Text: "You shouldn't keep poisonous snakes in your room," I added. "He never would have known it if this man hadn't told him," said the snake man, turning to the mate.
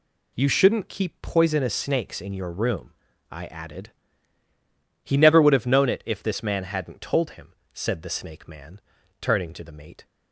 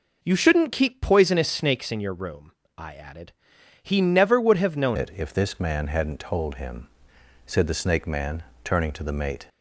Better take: first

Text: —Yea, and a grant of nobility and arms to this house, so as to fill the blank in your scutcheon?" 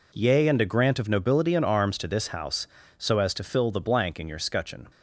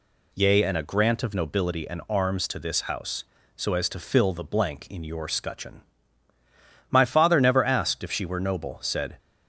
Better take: first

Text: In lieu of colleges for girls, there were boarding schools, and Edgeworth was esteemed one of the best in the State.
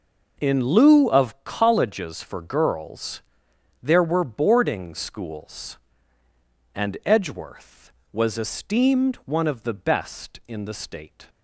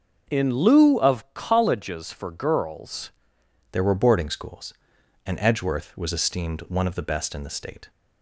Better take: first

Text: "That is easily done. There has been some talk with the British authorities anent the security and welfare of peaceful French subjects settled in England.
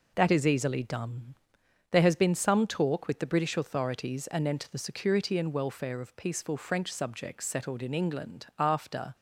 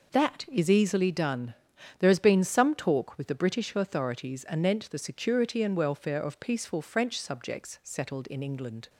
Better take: second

